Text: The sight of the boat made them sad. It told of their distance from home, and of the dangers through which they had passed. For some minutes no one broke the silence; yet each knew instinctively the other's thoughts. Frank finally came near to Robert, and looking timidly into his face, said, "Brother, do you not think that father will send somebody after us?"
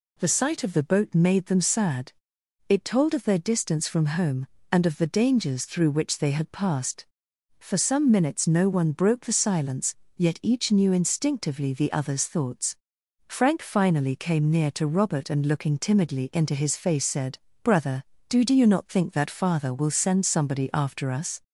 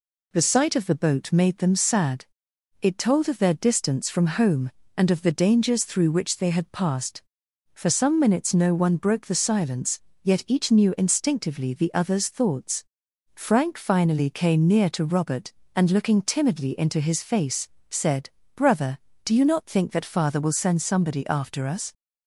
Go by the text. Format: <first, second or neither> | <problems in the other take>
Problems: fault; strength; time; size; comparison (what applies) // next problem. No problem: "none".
second | says "do" twice; at 18.4 s